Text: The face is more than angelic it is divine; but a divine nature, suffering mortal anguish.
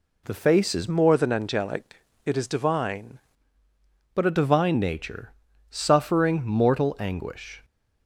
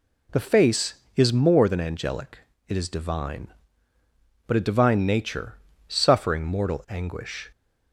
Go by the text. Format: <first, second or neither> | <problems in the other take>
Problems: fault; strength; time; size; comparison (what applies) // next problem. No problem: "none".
second | changes voice from "more" to "divine"; from 0.8 to 3.1 s; 2.3 s long // pauses between "angelic" and "it"; slight; at 2.0 s; 0.24 s long; slight in the second